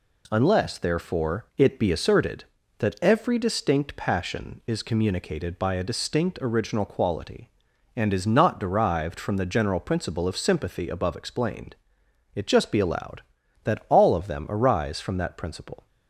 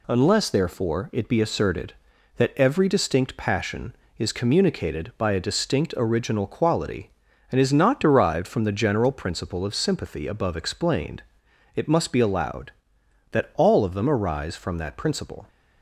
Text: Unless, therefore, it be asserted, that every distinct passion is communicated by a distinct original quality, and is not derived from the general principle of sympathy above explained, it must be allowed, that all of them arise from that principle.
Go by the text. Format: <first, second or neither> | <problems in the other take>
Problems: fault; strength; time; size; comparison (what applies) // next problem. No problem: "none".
second | says "just" for "must"; at 12.4 s